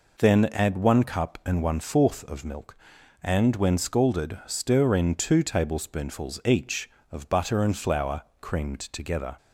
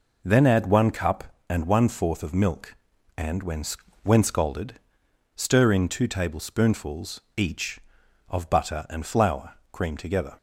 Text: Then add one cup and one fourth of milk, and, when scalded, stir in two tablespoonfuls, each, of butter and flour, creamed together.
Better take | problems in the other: first | says "when" twice; at 4.0 s

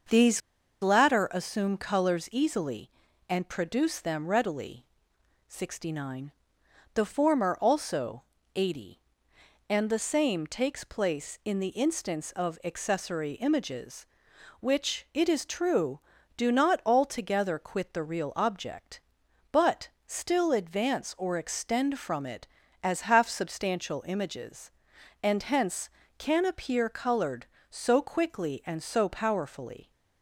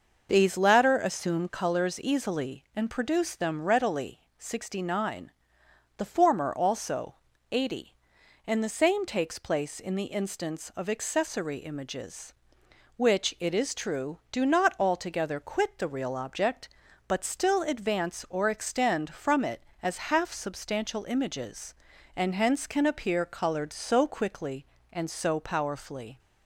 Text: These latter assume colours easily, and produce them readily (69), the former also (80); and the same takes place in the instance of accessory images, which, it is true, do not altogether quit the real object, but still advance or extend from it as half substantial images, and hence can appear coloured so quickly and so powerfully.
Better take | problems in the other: second | starts louder than the rest; until 1.5 s; 6.5 dB; noticeable in the second // pauses between "These" and "latter"; at 0.3 s; 0.42 s long // pauses between "but" and "still"; slight; at 19.8 s; 0.18 s long

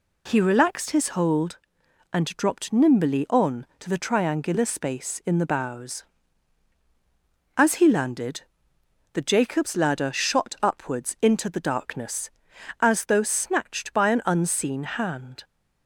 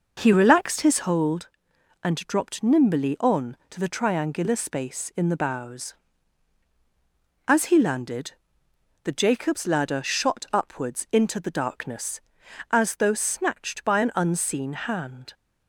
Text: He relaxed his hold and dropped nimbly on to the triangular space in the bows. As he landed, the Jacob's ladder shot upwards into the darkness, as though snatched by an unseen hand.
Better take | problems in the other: first | starts louder than the rest; noticeable; until 1.1 s; 5.5 dB

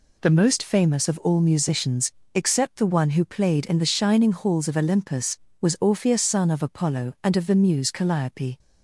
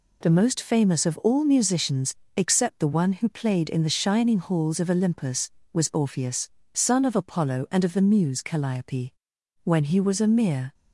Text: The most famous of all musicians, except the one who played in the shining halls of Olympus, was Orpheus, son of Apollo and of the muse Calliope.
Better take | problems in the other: first | goes on to say "When he was a mere"; noticeable; from 9.6 s on; 1.1 s long

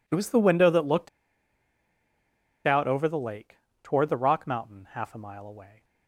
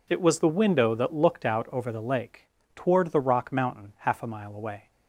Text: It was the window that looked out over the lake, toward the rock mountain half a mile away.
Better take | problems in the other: second | pauses between "looked" and "out"; strong; at 1.0 s; 1.5 s long

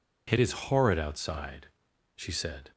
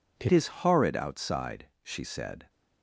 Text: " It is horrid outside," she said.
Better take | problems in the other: first | changes voice at "is"; from 0.2 s on; 2.2 s long

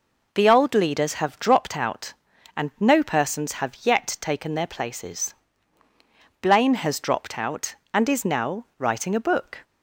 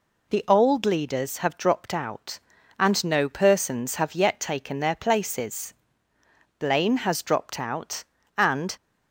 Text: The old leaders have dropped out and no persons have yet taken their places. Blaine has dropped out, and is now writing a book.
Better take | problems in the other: first | stops before "is now writing a book"; at 8.7 s

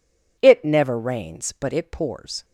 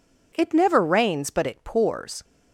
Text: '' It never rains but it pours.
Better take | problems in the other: neither | none

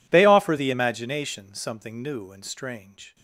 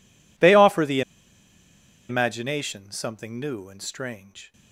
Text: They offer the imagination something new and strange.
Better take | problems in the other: first | pauses between "the" and "imagination"; at 1.0 s; 1.0 s long

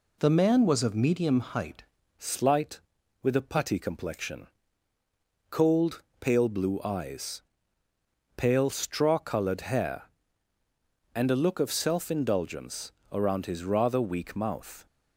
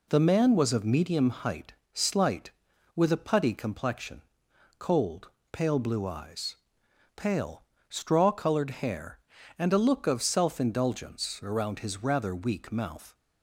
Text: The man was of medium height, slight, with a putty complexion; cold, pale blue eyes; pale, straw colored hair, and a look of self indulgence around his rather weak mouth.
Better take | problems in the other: second | changes voice at "slight"; from 2.1 s on; 12.7 s long // pauses between "indulgence" and "around"; slight; at 12.9 s; 0.20 s long

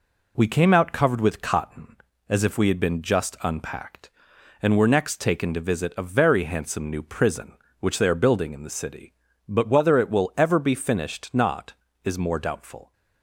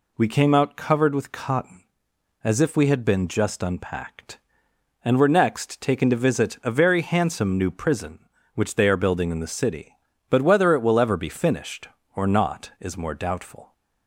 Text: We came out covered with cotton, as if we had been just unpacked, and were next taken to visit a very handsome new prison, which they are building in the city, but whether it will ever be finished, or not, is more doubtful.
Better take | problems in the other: second | skips "or"; at 11.3 s

